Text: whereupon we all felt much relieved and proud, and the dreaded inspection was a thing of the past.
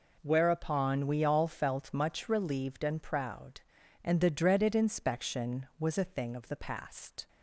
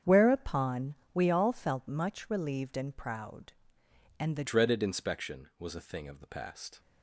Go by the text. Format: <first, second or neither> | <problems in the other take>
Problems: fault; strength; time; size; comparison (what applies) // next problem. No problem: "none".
first | starts louder than the rest; strong; until 1.2 s; 8 dB // pauses between "whereupon" and "we"; slight; at 0.9 s; 0.20 s long // changes voice at "dreaded"; from 4.4 s on; 2.3 s long